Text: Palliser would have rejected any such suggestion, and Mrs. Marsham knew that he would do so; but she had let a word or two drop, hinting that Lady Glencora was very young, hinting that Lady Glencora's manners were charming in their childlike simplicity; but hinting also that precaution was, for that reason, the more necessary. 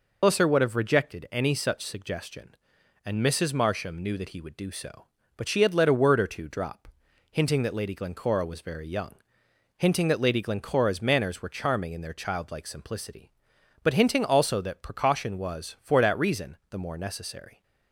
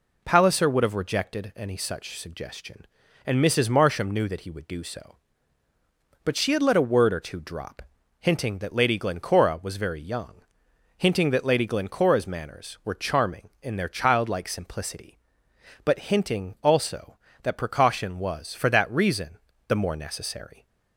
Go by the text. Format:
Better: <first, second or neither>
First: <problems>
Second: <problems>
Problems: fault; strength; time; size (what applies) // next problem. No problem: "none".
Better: second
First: loses the start of "Palliser"; at 0.2 s; 165 ms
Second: none